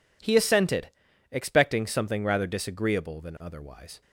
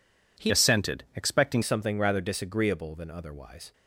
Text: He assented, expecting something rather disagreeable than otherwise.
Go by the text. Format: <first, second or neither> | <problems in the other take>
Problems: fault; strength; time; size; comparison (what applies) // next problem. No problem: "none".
first | changes voice from "assented" to "expecting"; from 0.4 to 1.6 s; 1.2 s long